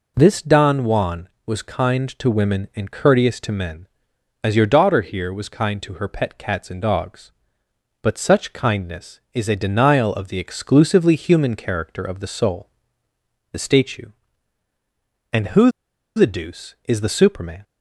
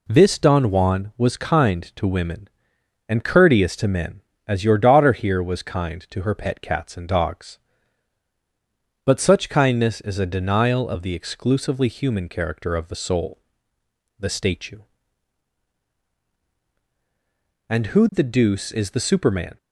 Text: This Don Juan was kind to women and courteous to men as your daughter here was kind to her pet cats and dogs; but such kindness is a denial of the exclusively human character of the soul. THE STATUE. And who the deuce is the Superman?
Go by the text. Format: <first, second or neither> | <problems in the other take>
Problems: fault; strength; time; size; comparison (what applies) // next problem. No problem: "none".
second | pauses between "who" and "the"; noticeable; at 15.6 s; 0.47 s long